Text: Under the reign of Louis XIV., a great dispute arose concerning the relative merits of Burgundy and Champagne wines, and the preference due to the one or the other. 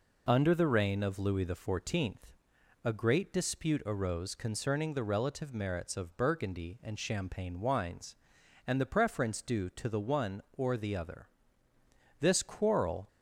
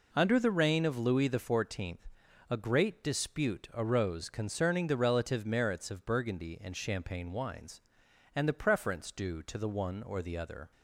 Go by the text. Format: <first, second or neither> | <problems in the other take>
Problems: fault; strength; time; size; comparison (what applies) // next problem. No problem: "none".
second | goes on to say "This quarrel"; noticeable; from 12.1 s on; 0.88 s long